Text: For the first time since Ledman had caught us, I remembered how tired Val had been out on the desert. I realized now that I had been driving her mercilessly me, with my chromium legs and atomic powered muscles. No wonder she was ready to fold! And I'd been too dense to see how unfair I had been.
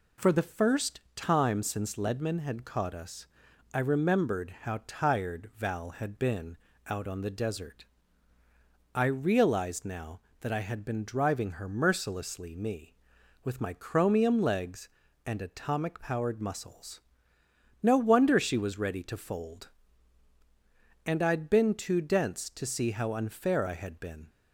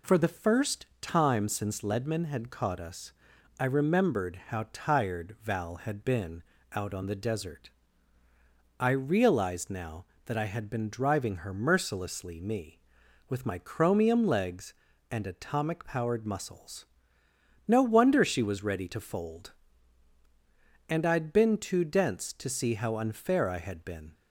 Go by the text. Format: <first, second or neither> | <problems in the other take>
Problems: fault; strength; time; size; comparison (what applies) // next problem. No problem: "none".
neither | pauses between "first" and "time"; slight; the same in both // pauses between "been" and "out"; slight; the same in both